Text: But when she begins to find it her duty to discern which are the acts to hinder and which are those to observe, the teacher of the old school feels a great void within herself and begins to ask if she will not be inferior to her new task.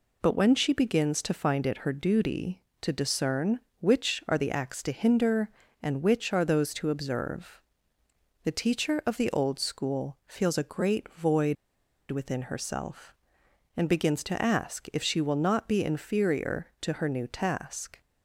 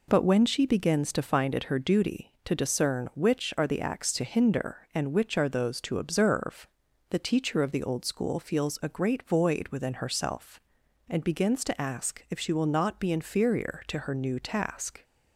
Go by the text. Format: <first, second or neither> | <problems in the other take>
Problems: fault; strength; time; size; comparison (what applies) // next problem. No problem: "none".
second | pauses between "void" and "within"; noticeable; at 11.5 s; 0.54 s long